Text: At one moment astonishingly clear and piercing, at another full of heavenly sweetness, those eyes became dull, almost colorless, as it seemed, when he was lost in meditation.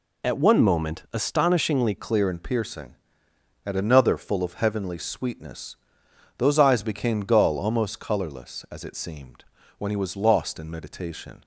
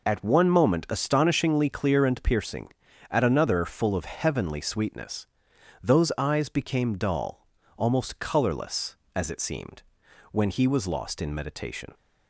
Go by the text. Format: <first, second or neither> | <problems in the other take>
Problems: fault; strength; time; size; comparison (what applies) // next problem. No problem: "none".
second | changes voice at "clear"; from 1.9 s on; 9.5 s long